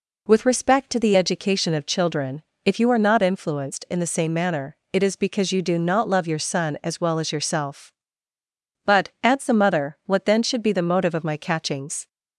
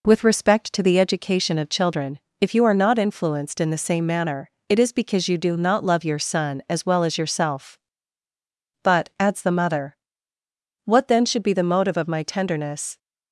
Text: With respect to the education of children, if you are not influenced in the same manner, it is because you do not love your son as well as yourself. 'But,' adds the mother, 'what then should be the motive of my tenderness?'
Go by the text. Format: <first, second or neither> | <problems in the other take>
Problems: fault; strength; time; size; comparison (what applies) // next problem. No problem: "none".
second | says "catchings" for "tenderness"; at 11.3 s